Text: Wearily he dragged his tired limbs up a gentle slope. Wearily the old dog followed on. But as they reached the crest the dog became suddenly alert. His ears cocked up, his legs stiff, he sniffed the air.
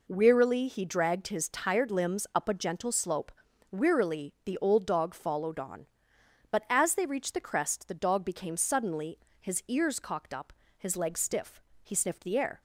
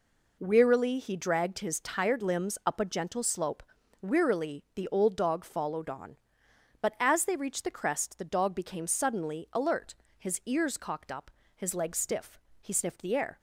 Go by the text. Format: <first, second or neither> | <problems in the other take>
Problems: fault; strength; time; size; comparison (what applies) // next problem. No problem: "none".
second | skips "alert"; at 9.2 s